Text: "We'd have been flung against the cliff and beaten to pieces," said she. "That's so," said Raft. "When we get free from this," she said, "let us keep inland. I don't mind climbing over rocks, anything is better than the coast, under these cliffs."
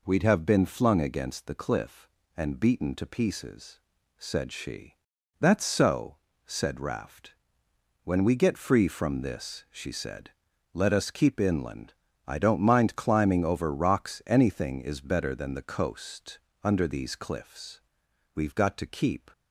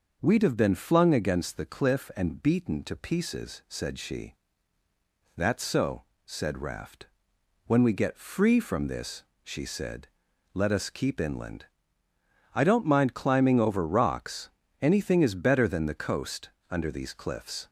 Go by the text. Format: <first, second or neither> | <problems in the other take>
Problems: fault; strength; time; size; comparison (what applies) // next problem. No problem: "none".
second | goes on to say "We've got to keep"; noticeable; from 18.3 s on; 0.96 s long